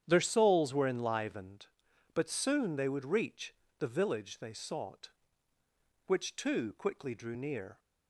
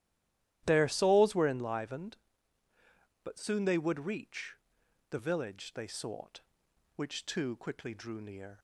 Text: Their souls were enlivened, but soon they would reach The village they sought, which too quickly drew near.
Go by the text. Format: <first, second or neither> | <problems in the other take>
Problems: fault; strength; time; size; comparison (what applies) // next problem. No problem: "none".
first | stays silent before the first word; slight; until 0.6 s; 0.6 s long // starts louder than the rest; strong; until 1.6 s; 12.5 dB; strong in the first // pauses between "reach" and "The"; noticeable; at 4.5 s; 0.54 s long; slight in the first